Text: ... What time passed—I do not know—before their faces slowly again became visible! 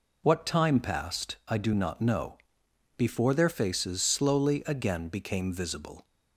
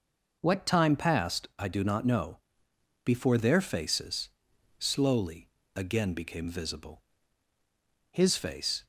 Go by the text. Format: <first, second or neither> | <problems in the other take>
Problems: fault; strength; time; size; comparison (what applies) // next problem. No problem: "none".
first | pauses between "faces" and "slowly"; noticeable; at 4.2 s; 0.50 s long // pauses between "slowly" and "again"; slight; at 5.4 s; 0.26 s long // goes on to say "His face"; noticeable; from 8.1 s on; 0.74 s long